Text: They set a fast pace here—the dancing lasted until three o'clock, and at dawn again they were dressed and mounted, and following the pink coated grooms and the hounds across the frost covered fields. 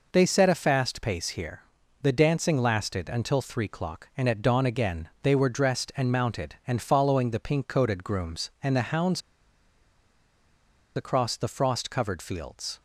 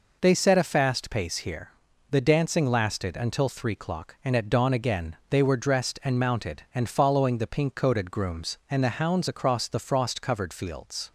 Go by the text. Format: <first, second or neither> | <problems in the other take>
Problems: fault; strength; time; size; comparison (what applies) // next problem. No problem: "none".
second | pauses between "hounds" and "across"; strong; at 9.2 s; 1.7 s long